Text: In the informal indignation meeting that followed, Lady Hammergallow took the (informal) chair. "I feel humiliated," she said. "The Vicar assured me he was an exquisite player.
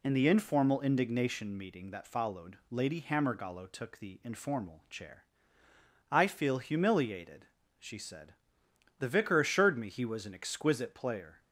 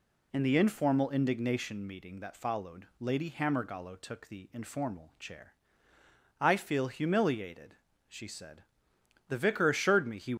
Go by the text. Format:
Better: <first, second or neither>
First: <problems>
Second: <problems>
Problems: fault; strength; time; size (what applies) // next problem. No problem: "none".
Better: first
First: none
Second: stops before "was an exquisite player"; at 10.3 s